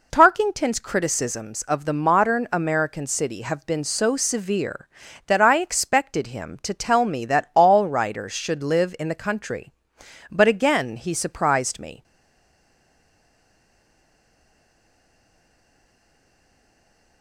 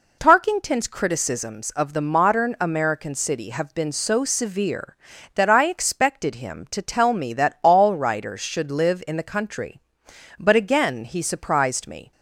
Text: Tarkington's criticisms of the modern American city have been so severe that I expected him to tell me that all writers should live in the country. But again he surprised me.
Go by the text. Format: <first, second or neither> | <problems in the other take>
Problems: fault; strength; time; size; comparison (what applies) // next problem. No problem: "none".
second | stays silent after the last word; strong; from 12.0 s on; 5.2 s long